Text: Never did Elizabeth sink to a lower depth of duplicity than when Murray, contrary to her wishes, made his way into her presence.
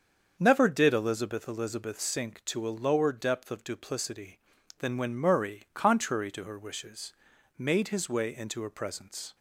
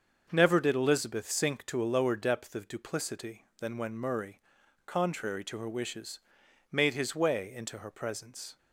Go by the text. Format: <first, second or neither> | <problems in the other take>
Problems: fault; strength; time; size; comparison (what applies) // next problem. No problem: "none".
second | starts louder than the rest; until 1.3 s; 7 dB; also in the second // says "Elizabeth" twice; at 1.4 s